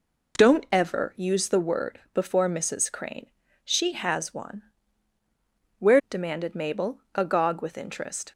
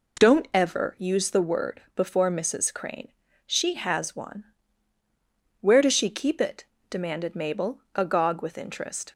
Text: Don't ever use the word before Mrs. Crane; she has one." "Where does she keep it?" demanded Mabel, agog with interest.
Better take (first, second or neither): second